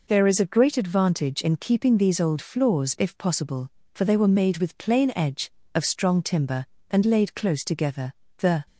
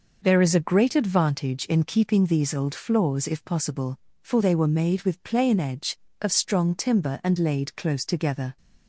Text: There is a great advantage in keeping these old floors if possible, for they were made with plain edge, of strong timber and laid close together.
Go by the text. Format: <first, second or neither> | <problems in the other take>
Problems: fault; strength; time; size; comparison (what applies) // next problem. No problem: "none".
second | goes on to say "The"; slight; from 8.3 s on; 0.26 s long